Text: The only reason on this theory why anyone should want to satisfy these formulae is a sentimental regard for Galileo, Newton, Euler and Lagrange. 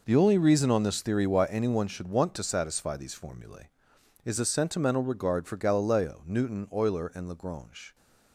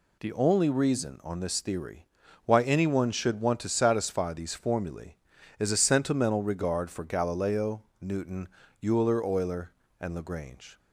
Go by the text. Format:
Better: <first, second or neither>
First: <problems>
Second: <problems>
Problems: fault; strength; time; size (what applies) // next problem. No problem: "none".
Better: first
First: none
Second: pauses between "theory" and "why"; at 2.0 s; 0.40 s long // says "Euler" twice; at 9.2 s